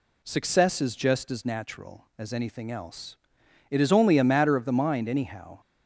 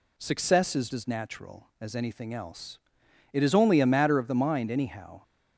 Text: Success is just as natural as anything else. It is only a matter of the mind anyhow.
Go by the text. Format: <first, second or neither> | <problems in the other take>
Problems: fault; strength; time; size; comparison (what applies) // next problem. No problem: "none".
first | skips "just"; at 0.9 s